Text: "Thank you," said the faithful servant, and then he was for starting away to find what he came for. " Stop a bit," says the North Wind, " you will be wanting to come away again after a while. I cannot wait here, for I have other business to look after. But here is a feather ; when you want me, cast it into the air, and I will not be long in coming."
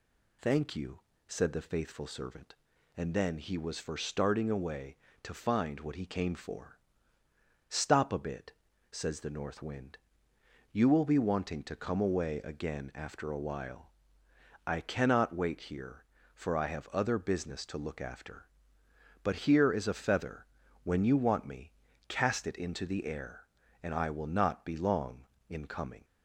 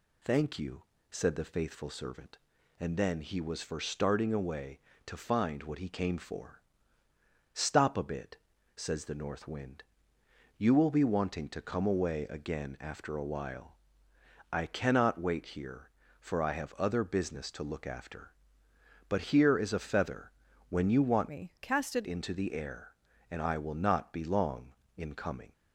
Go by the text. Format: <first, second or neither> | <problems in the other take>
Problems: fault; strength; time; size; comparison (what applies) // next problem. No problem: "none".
first | changes voice from "me" to "it"; from 21.2 to 22.0 s; 0.8 s long